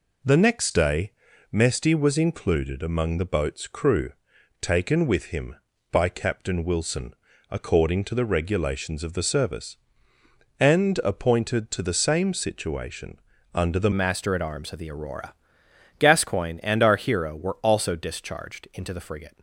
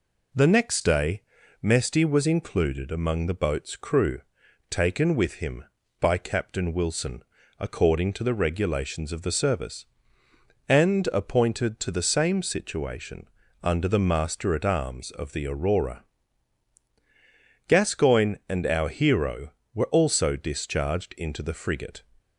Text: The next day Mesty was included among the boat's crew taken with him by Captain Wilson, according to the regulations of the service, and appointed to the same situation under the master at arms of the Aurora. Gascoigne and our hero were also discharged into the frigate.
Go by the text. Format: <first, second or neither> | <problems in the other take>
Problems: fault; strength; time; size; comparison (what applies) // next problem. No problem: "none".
second | pauses between "day" and "Mesty"; at 1.1 s; 0.38 s long; also in the second // pauses between "crew" and "taken"; noticeable; at 4.1 s; 0.48 s long; noticeable in the second // pauses between "situation" and "under"; slight; at 13.1 s; 0.34 s long; slight in the second // changes voice at "master"; from 13.9 s on; 5.4 s long